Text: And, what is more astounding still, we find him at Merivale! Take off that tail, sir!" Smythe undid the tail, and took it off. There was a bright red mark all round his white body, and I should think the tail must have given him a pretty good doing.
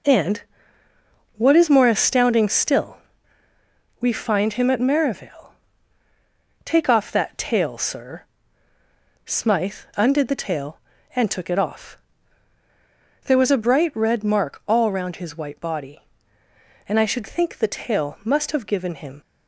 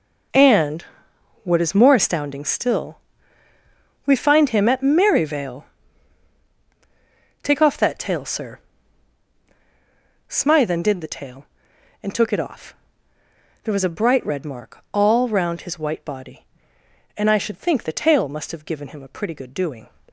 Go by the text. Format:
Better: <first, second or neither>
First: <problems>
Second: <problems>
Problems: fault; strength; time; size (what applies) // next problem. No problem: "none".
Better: second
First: stops before "a pretty good doing"; at 19.2 s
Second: none